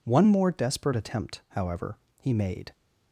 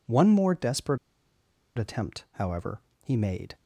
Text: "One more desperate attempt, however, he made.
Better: first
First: none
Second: pauses between "desperate" and "attempt"; noticeable; at 0.9 s; 0.80 s long

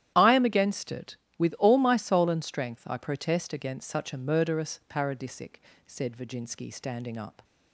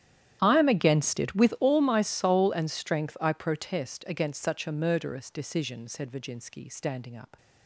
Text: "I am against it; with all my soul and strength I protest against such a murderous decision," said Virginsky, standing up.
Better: second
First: starts louder than the rest; strong; until 1.1 s; 11.5 dB // says "paradisic" for "decision"; at 4.8 s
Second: starts louder than the rest; strong; until 1.4 s; 11 dB

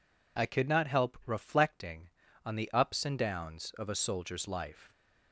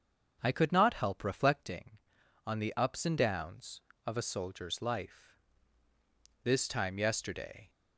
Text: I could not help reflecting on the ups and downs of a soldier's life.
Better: first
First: none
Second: starts louder than the rest; until 1.4 s; 6.5 dB // goes on to say "This time yesterday"; noticeable; from 6.4 s on; 1.2 s long

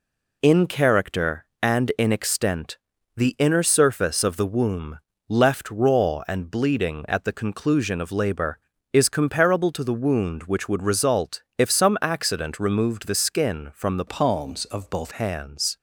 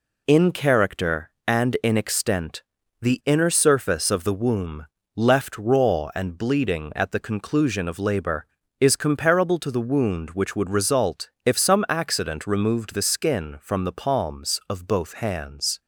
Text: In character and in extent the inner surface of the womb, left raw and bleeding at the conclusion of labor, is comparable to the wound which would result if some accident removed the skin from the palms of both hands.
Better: second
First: pauses between "extent" and "the"; at 2.7 s; 0.40 s long // changes voice from "palms" to "both"; from 14.0 to 15.1 s; 1.1 s long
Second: pauses between "extent" and "the"; at 2.6 s; 0.40 s long

